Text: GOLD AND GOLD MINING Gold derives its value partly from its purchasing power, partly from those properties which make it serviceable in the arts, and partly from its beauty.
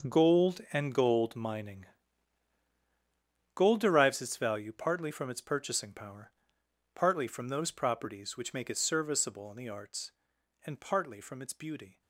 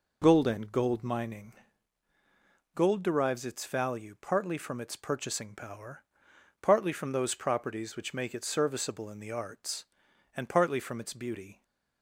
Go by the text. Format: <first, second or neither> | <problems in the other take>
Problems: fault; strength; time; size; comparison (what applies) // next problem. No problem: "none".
second | gets quieter; strong; throughout; 13 dB // pauses between "MINING" and "Gold"; strong; at 1.8 s; 1.6 s long; also in the second